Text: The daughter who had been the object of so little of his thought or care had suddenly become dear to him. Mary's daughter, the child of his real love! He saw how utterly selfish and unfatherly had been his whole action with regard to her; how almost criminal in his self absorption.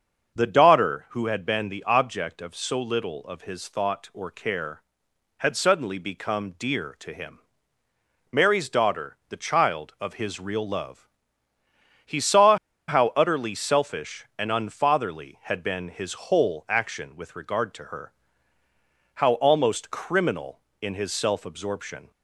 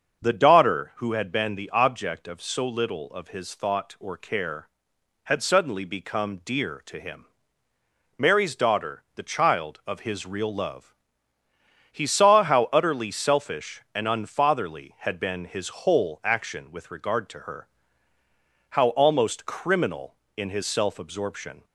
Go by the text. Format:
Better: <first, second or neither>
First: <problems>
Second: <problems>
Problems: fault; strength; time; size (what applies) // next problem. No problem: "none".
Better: second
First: starts louder than the rest; until 1.4 s; 6.5 dB // pauses between "saw" and "how"; slight; at 12.5 s; 0.31 s long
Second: starts louder than the rest; until 1.2 s; 6.5 dB